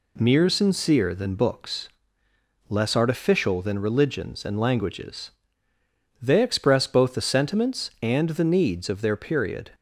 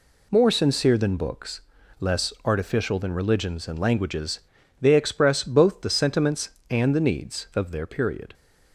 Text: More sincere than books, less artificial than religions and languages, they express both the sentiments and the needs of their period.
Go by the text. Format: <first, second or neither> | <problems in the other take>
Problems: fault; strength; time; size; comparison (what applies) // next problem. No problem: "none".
second | says "Mere" for "More"; at 0.1 s